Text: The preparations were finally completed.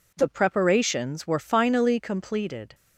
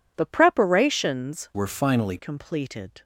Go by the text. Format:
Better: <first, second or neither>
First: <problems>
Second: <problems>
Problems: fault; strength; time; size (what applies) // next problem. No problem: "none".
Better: first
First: none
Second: changes voice from "were" to "finally"; from 1.5 to 2.1 s; 0.6 s long